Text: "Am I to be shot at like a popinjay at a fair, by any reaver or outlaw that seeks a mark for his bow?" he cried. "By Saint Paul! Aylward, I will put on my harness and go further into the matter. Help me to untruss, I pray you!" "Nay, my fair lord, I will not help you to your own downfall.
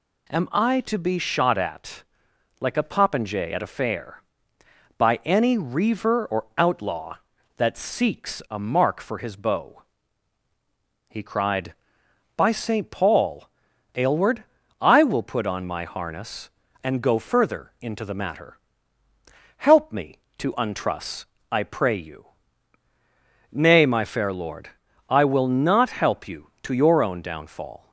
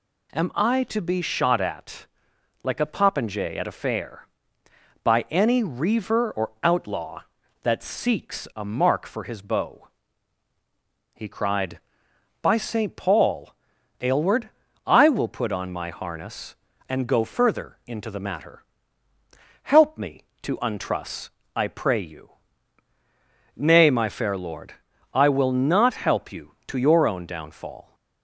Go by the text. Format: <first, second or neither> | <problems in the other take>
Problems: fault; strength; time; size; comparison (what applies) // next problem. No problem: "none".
neither | pauses between "at" and "like"; noticeable; the same in both